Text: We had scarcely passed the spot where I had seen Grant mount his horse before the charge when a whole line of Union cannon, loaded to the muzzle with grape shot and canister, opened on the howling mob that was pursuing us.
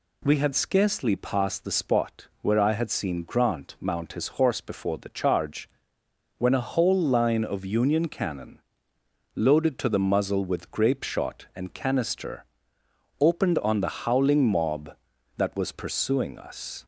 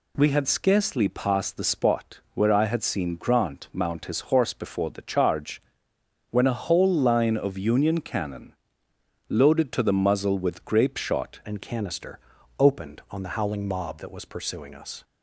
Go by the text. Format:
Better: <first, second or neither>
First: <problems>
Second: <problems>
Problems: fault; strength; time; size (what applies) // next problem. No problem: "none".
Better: first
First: pauses between "charge" and "when"; noticeable; at 5.6 s; 0.70 s long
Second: pauses between "charge" and "when"; noticeable; at 5.5 s; 0.70 s long // changes voice at "and"; from 11.4 s on; 3.6 s long